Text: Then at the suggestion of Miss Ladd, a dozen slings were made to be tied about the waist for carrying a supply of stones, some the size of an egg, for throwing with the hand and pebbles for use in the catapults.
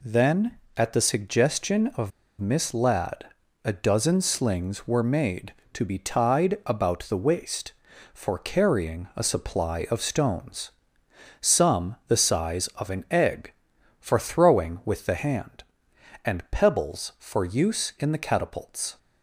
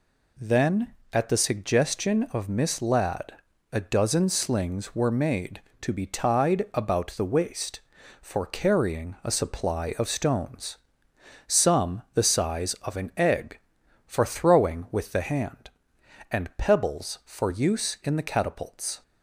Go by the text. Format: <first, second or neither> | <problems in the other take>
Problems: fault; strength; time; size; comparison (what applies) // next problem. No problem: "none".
second | pauses between "of" and "Miss"; slight; at 2.1 s; 0.29 s long